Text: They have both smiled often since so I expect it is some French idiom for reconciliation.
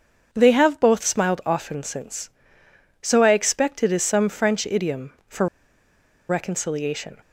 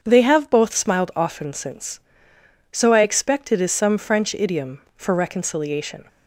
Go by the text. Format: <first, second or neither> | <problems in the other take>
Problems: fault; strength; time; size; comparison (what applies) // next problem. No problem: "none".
second | starts louder than the rest; until 1.3 s; 7 dB; strong in the second // pauses between "for" and "reconciliation"; noticeable; at 5.4 s; 0.81 s long